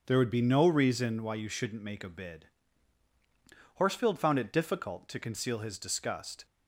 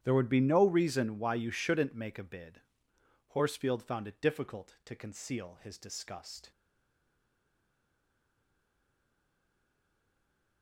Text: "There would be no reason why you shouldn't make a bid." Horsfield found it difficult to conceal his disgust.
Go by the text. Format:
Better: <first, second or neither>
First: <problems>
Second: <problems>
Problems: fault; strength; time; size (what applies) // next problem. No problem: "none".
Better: first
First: starts louder than the rest; until 1.0 s; 7 dB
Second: starts louder than the rest; strong; until 1.0 s; 10.5 dB // stays silent after the last word; strong; from 6.5 s on; 4.1 s long